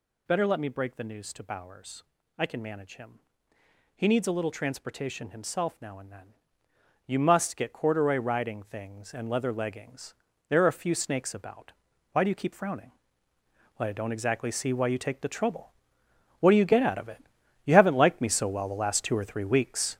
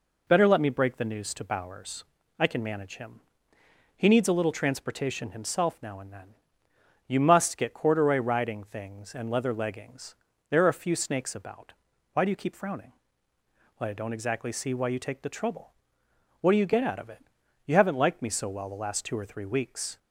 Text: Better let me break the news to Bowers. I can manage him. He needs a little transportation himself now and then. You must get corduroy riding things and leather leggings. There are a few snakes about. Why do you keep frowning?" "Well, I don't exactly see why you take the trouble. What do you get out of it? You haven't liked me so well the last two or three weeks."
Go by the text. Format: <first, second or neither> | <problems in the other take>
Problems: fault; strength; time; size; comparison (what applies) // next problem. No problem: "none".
second | gets louder; strong; throughout; 8 dB